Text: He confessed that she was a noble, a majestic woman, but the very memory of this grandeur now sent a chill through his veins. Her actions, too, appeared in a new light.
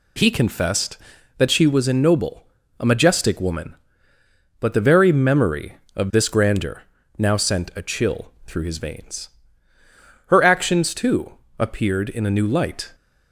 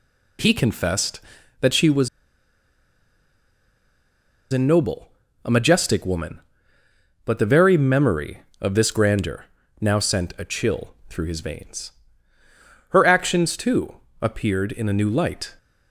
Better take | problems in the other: first | pauses between "was" and "a"; strong; at 2.0 s; 2.4 s long // pauses between "grandeur" and "now"; slight; at 9.4 s; 0.36 s long; slight in the first // pauses between "chill" and "through"; slight; at 10.9 s; 0.16 s long; slight in the first

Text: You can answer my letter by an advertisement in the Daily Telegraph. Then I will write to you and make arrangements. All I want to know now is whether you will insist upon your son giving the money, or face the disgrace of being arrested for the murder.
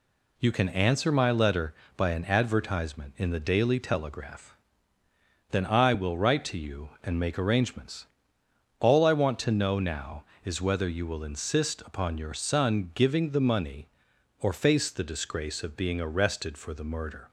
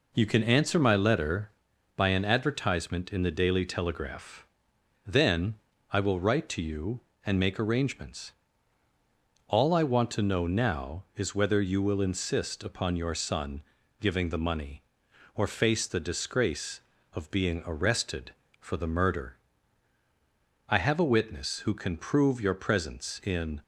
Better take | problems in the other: first | pauses between "Then" and "I"; slight; at 5.5 s; 0.36 s long // pauses between "son" and "giving"; at 13.6 s; 0.38 s long // goes on to say "I have a witness who can prove your presence in"; strong; from 20.6 s on; 2.9 s long

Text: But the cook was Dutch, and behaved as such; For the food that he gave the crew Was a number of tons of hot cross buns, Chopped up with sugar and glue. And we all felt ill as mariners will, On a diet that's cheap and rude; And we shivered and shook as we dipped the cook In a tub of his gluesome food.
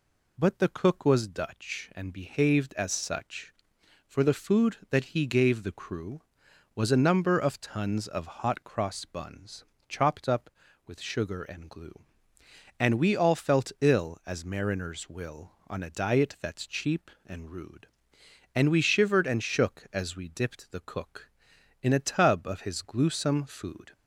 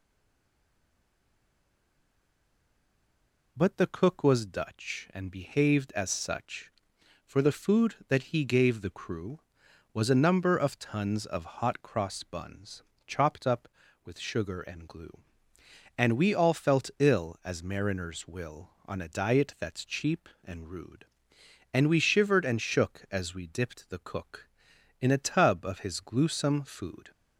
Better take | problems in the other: first | stays silent before the first word; strong; until 3.5 s; 3.5 s long

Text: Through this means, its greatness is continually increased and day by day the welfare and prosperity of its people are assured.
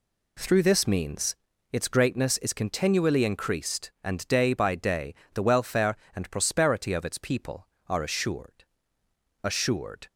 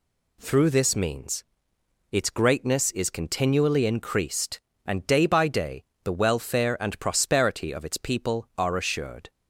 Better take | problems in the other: second | pauses between "day" and "the"; slight; at 5.1 s; 0.18 s long; slight in the second // says "assured" twice; at 9.4 s

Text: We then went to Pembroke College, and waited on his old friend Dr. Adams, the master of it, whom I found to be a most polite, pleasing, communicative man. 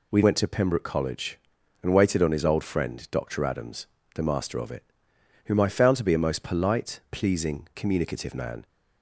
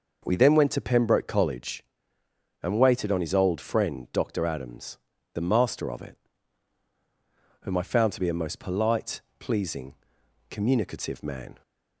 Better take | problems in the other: second | skips "then"; at 0.2 s

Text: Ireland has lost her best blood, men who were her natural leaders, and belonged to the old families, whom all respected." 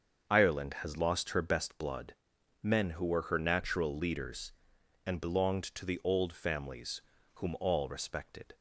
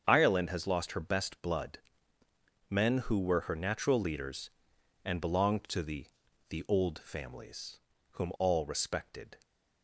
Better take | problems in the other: first | starts louder than the rest; strong; until 1.0 s; 7.5 dB; also in the first // says "the" twice; at 6.4 s

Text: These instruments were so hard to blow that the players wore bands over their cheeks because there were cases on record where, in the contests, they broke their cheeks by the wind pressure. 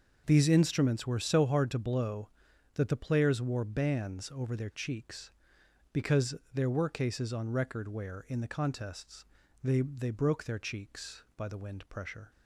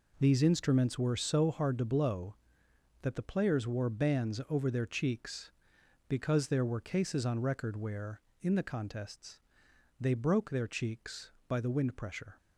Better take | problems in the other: second | pauses between "because" and "there"; slight; at 6.3 s; 0.18 s long // says "they" twice; at 9.8 s

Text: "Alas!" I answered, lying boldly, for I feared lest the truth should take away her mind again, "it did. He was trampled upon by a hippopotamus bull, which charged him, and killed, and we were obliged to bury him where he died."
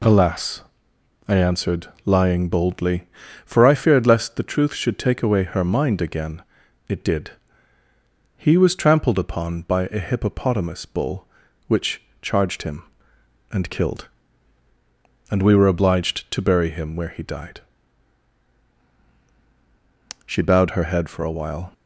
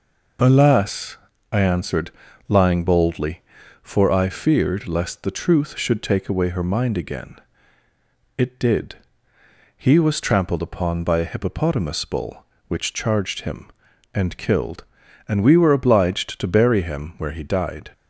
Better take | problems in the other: second | pauses between "which" and "charged"; slight; at 12.0 s; 0.18 s long // goes on to say "She bowed her head for a while"; from 20.2 s on; 1.4 s long

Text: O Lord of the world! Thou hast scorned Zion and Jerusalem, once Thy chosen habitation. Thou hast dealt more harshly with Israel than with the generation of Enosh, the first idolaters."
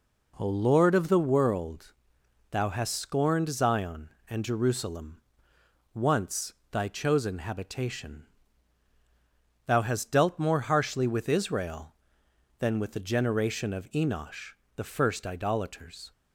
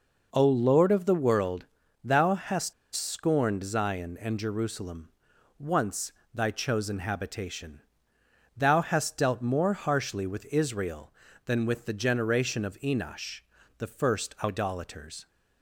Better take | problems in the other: first | pauses between "hast" and "scorned"; slight; at 2.7 s; 0.21 s long // pauses between "once" and "Thy"; slight; at 6.1 s; 0.22 s long; slight in the first

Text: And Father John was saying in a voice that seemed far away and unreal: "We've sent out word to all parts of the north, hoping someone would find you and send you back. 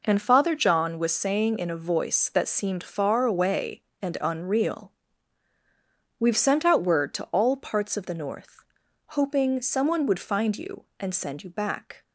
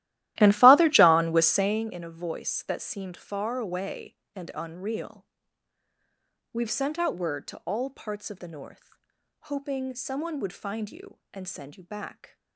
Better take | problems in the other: first | starts louder than the rest; strong; until 1.9 s; 15 dB

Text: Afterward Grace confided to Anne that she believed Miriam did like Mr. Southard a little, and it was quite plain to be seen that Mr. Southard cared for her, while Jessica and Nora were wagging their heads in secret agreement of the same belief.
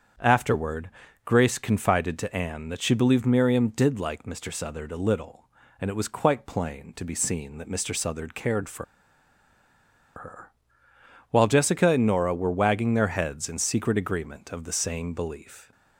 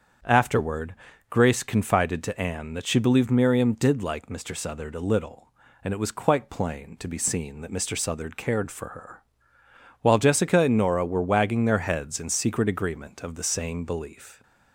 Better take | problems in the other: second | starts louder than the rest; strong; until 1.5 s; 7.5 dB; strong in the second // pauses between "Afterward" and "Grace"; slight; at 0.8 s; 0.34 s long; slight in the second // pauses between "for" and "her"; strong; at 8.8 s; 1.3 s long

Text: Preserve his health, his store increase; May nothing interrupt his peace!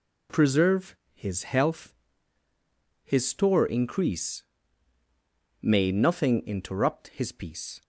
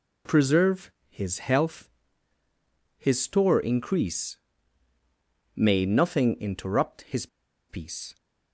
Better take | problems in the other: first | pauses between "Preserve" and "his"; slight; at 0.9 s; 0.18 s long; slight in the first // pauses between "his" and "peace"; at 7.2 s; 0.42 s long

